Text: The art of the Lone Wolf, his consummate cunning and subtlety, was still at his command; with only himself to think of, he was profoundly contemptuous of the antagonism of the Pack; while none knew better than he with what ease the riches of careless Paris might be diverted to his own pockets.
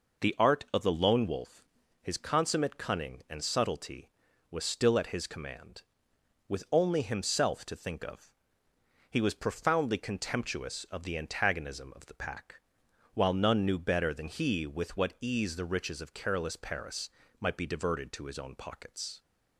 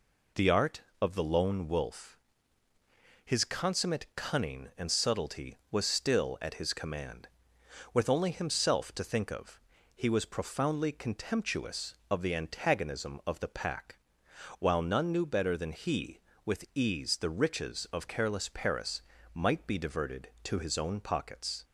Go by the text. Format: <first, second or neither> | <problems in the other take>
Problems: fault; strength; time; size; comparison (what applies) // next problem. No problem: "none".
first | skips "what"; at 16.6 s // pauses between "Paris" and "might"; slight; at 19.0 s; 0.32 s long; slight in the first